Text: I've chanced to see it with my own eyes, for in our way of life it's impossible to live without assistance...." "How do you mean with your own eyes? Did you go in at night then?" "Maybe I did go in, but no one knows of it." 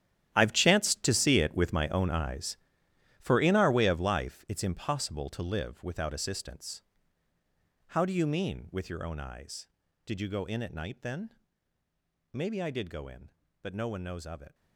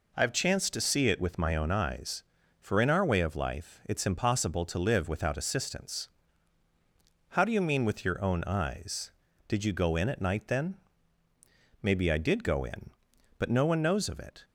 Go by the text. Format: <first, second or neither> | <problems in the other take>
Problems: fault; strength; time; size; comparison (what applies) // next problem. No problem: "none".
second | gets quieter; strong; throughout; 15 dB